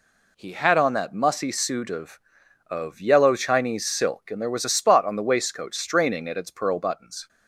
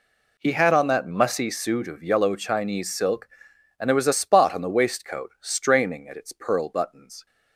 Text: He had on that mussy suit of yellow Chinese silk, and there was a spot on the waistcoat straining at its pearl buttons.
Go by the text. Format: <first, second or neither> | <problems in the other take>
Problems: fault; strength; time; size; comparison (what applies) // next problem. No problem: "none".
second | says "of" twice; at 2.6 s